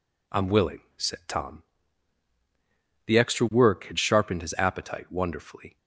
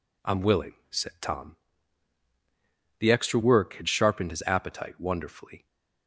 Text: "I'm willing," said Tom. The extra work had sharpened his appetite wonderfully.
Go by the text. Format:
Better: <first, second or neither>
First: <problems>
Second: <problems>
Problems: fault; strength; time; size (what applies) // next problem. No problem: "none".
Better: neither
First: none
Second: none